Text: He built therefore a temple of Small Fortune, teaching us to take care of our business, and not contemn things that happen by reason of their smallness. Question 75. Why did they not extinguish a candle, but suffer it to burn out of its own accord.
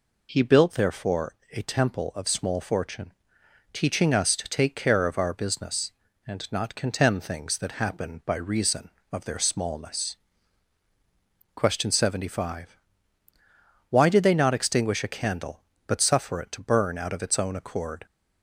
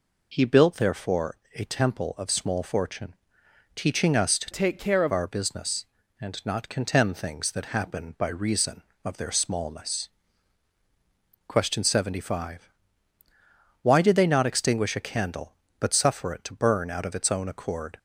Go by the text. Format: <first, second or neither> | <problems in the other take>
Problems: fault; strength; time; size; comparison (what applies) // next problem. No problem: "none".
first | pauses between "therefore" and "a"; slight; at 1.3 s; 0.20 s long; slight in the first // changes voice from "take" to "of"; from 4.5 to 5.1 s; 0.6 s long